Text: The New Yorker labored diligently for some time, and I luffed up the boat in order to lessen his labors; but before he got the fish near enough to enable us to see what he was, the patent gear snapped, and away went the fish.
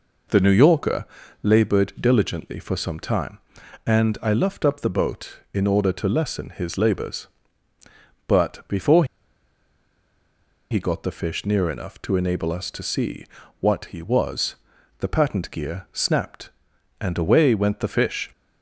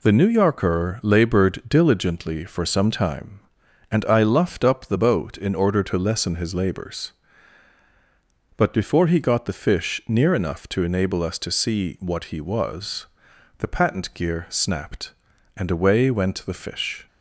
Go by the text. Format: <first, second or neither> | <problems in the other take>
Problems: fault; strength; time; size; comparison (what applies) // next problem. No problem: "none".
second | pauses between "Yorker" and "labored"; slight; at 1.0 s; 0.36 s long // pauses between "before" and "he"; strong; at 9.0 s; 1.6 s long // pauses between "see" and "what"; slight; at 13.2 s; 0.34 s long